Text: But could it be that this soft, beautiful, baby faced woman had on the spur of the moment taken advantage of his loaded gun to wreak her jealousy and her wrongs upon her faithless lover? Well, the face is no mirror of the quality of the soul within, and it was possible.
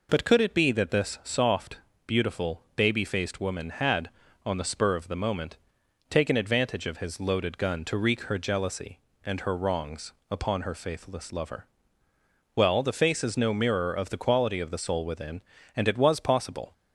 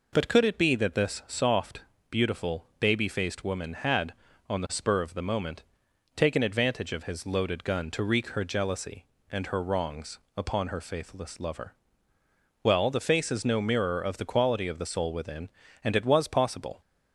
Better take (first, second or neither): neither